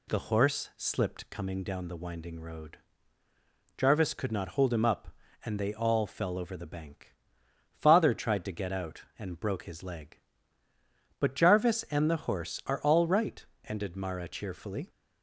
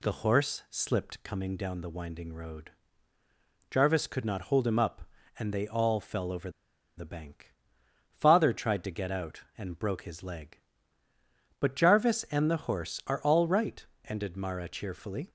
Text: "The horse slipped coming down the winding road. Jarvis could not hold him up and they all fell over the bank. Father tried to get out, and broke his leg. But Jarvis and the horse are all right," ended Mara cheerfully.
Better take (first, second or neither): first